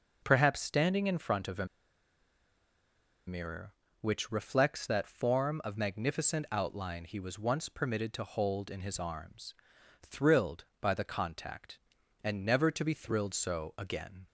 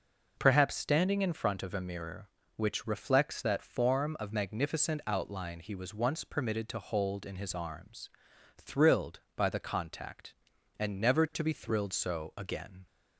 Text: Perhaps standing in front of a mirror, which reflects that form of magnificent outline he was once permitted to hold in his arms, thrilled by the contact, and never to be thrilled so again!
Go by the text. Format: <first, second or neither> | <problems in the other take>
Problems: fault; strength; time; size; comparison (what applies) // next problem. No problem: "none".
second | pauses between "a" and "mirror"; strong; at 1.6 s; 1.6 s long